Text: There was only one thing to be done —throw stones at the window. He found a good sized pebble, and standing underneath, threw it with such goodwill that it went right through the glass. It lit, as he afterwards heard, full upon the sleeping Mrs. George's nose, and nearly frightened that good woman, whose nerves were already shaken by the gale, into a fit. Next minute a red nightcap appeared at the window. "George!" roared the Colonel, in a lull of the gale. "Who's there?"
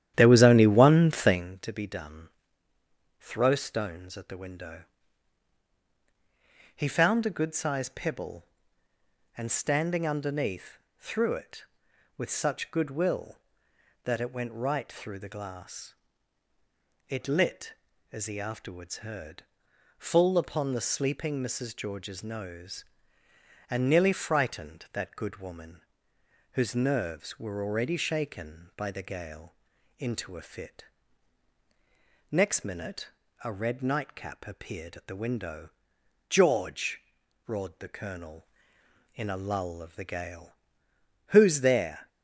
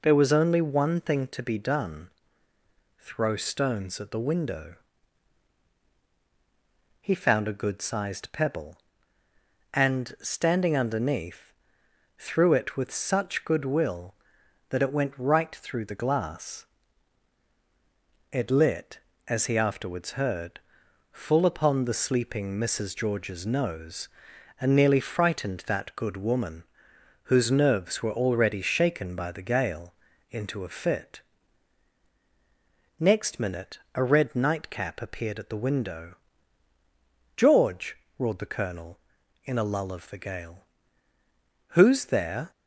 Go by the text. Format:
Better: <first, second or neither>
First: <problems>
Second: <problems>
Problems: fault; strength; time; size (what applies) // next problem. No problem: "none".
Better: second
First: starts louder than the rest; strong; until 1.5 s; 11 dB // pauses between "minute" and "a"; slight; at 33.0 s; 0.34 s long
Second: pauses between "minute" and "a"; slight; at 33.7 s; 0.16 s long